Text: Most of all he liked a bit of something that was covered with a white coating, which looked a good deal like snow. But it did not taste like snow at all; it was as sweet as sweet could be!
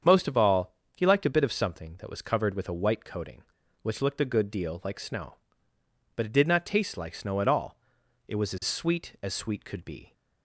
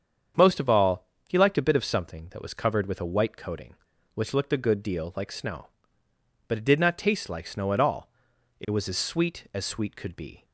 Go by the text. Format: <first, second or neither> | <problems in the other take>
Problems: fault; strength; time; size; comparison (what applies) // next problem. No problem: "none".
neither | starts louder than the rest; strong; the same in both // pauses between "all" and "he"; slight; the same in both